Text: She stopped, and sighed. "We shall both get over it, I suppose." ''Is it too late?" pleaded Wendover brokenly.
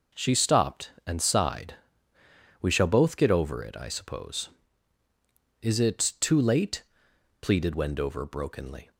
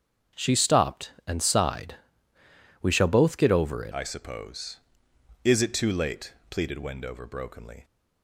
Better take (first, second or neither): first